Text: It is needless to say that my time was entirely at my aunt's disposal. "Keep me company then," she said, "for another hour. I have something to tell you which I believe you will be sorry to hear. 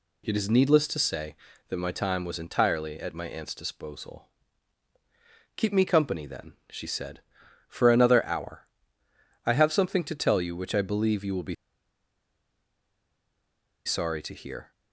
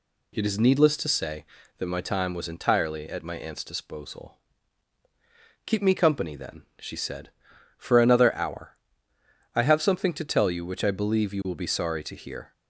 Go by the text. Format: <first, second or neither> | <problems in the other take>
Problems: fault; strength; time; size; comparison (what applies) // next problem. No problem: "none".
second | pauses between "be" and "sorry"; strong; at 11.5 s; 2.3 s long